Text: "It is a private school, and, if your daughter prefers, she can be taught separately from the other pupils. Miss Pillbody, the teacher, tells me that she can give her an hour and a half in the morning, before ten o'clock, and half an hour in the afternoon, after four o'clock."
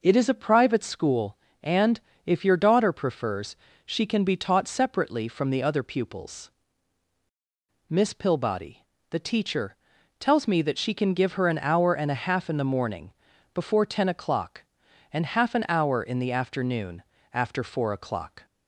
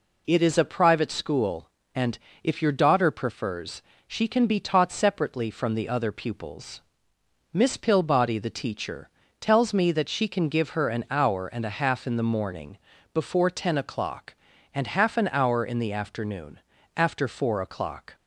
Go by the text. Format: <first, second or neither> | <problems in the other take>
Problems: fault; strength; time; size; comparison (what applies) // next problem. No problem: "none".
neither | none